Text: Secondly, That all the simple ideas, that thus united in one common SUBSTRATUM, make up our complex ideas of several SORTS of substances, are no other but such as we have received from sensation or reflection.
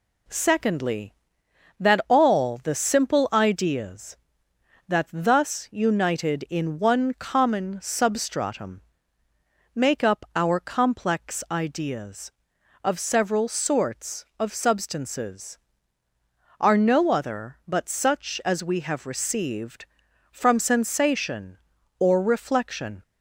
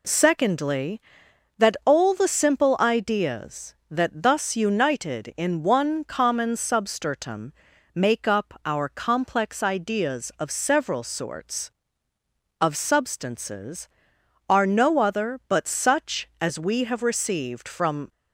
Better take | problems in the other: first | stops before "sensation or reflection"; at 18.0 s

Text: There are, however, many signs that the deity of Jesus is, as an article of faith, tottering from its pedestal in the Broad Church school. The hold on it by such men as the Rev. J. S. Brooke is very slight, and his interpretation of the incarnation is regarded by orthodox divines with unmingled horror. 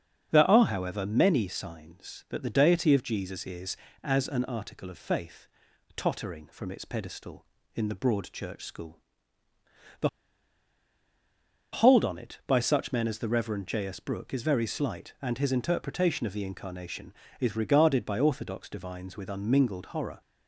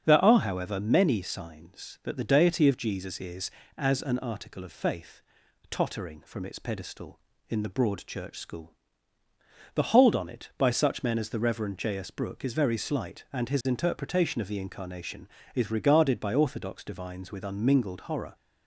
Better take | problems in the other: second | starts louder than the rest; strong; until 1.3 s; 7.5 dB; strong in the second // pauses between "The" and "hold"; strong; at 10.0 s; 1.6 s long

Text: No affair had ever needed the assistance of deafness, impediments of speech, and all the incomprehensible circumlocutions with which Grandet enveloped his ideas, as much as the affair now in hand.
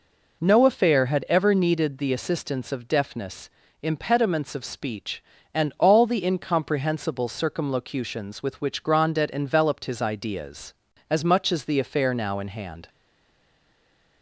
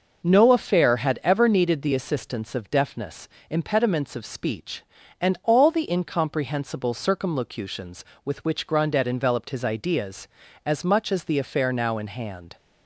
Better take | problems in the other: second | stays silent after the last word; noticeable; from 12.8 s on; 1.4 s long

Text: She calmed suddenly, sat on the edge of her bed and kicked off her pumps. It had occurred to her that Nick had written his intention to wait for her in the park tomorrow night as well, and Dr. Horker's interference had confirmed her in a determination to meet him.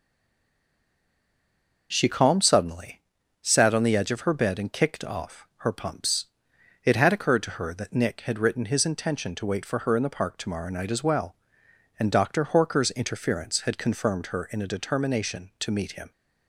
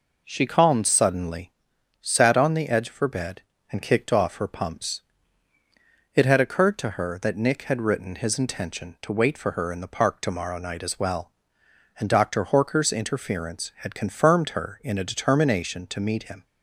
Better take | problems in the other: second | stays silent before the first word; noticeable; until 1.9 s; 1.9 s long

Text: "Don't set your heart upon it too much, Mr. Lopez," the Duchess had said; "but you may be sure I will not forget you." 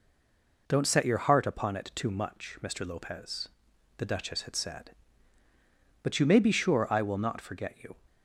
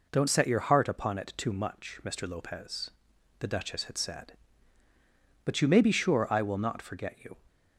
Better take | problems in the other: second | stays silent before the first word; slight; until 0.6 s; 0.6 s long

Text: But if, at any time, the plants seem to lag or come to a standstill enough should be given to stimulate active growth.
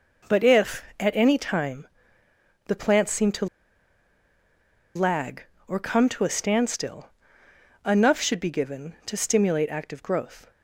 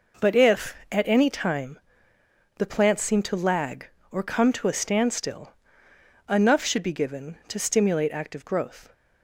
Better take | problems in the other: second | pauses between "to" and "lag"; strong; at 3.4 s; 1.4 s long // pauses between "standstill" and "enough"; noticeable; at 7.0 s; 0.78 s long; noticeable in the second

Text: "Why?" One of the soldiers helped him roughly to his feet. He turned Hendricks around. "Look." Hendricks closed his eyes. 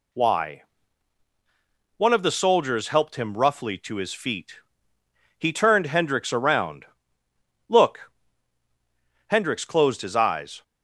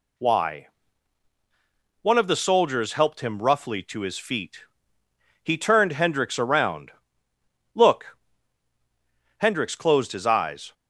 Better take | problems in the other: neither | none

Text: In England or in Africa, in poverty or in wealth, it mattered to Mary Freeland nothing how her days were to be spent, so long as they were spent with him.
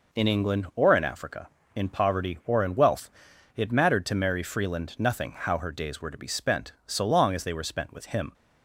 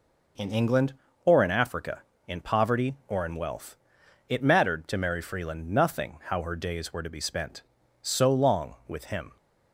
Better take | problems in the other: first | skips "as they were spent"; at 8.8 s

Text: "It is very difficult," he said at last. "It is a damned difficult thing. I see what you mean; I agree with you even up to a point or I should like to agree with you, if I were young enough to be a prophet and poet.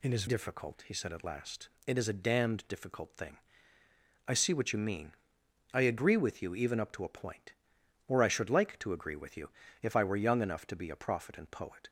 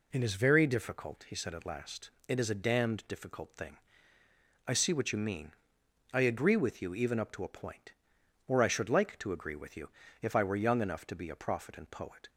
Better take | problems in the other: second | skips "very"; at 0.2 s

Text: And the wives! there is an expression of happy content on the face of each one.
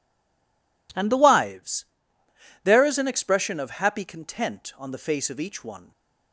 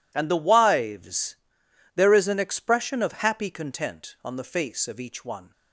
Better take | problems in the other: second | stays silent before the first word; slight; until 0.8 s; 0.8 s long

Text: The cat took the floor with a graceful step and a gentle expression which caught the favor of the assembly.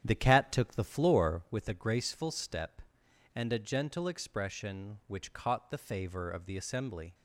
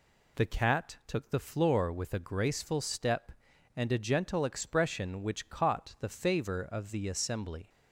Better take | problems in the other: second | starts louder than the rest; strong; until 1.5 s; 9.5 dB

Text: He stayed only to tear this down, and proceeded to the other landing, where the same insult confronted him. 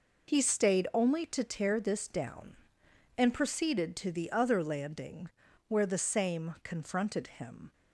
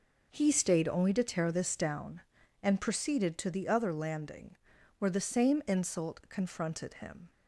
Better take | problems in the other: second | skips "insult"; at 6.5 s

